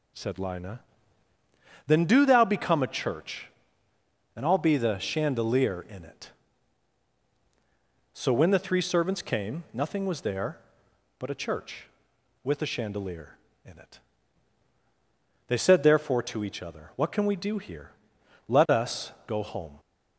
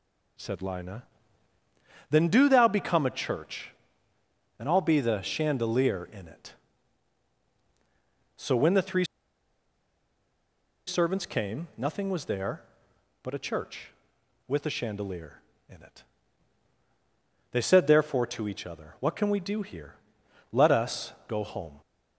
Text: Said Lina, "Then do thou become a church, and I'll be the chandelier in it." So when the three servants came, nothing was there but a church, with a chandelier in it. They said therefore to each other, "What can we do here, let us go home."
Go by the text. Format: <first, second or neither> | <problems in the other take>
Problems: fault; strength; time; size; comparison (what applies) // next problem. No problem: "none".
first | pauses between "three" and "servants"; strong; at 9.0 s; 1.8 s long // pauses between "us" and "go"; slight; at 21.1 s; 0.16 s long; slight in the first